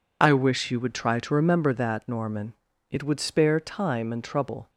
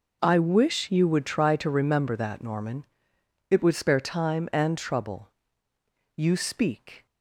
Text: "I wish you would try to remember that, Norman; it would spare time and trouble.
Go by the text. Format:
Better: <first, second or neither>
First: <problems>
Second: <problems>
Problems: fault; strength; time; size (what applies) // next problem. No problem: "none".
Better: first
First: none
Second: goes on to say "You speak"; noticeable; from 6.1 s on; 0.88 s long